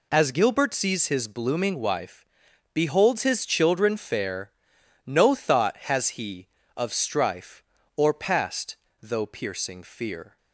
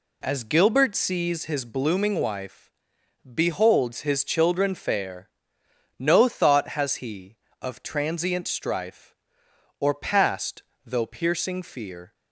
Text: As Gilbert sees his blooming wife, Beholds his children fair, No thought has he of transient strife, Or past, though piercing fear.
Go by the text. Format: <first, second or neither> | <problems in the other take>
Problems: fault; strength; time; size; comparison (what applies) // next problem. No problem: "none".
second | skips "transient"; at 6.9 s